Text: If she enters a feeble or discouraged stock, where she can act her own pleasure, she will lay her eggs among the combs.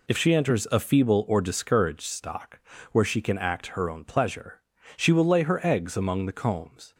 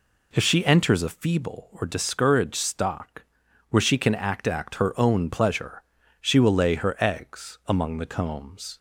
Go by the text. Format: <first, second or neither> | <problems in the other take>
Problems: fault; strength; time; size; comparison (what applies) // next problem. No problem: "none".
first | says "act" twice; at 4.4 s